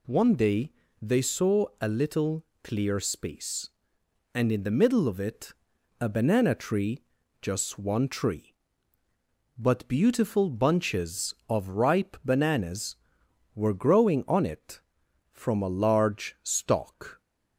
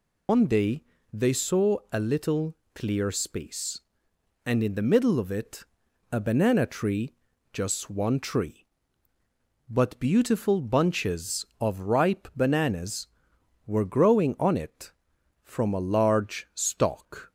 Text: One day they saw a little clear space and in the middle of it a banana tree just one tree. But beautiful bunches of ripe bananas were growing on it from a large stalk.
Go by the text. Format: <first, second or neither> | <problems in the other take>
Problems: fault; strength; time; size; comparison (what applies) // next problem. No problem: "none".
first | loses the start of "One"; at 0.2 s; 110 ms // pauses between "day" and "they"; slight; at 0.8 s; 0.30 s long; slight in the first // pauses between "little" and "clear"; slight; at 2.5 s; 0.18 s long; slight in the first // pauses between "it" and "a"; noticeable; at 5.6 s; 0.46 s long; noticeable in the first // pauses between "tree" and "just"; at 7.1 s; 0.40 s long; also in the first